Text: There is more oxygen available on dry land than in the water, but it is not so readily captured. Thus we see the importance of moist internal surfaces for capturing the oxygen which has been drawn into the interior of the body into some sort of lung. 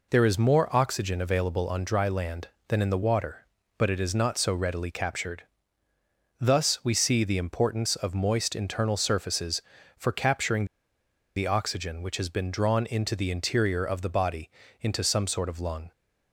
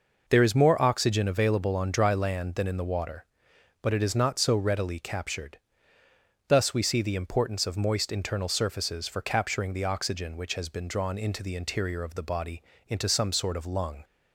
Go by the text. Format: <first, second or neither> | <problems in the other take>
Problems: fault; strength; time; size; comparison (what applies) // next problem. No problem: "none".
second | pauses between "capturing" and "the"; noticeable; at 10.6 s; 0.69 s long // pauses between "body" and "into"; slight; at 14.4 s; 0.32 s long; slight in the second